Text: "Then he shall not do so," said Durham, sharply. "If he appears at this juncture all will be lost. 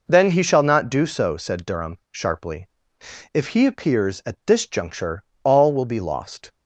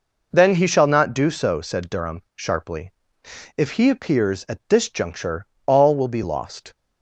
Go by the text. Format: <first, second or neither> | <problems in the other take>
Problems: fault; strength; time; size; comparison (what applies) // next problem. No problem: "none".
neither | pauses between "juncture" and "all"; slight; the same in both